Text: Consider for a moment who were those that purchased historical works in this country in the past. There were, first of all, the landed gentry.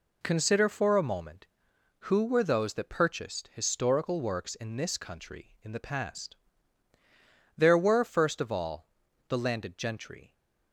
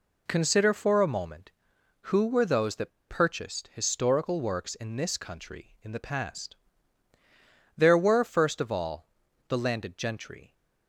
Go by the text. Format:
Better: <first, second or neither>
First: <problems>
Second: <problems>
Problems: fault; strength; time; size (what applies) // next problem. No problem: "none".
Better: first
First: none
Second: pauses between "that" and "purchased"; slight; at 2.9 s; 0.18 s long